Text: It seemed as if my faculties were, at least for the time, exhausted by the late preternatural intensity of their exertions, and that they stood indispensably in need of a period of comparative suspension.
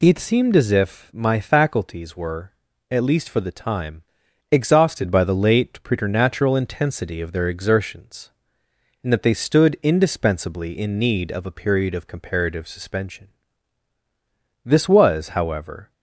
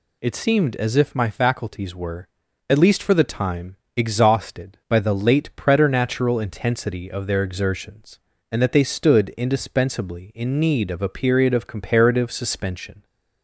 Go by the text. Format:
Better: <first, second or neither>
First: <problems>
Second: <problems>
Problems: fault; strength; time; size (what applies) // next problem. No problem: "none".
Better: second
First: goes on to say "This was however"; noticeable; from 14.6 s on; 1.2 s long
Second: none